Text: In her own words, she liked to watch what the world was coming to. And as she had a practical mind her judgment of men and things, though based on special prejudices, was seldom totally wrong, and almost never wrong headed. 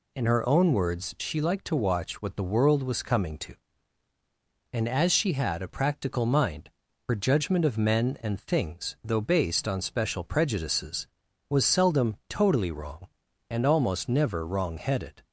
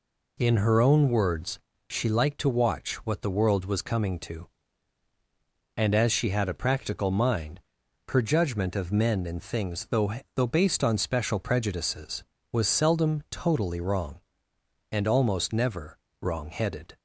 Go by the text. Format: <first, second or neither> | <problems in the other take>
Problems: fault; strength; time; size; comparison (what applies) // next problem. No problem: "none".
first | pauses between "mind" and "her"; noticeable; at 7.6 s; 0.48 s long; also in the first // says "though" twice; at 10.3 s // pauses between "never" and "wrong"; slight; at 15.9 s; 0.24 s long